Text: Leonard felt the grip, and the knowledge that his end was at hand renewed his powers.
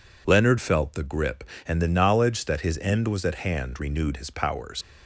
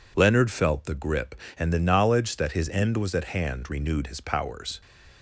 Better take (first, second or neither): second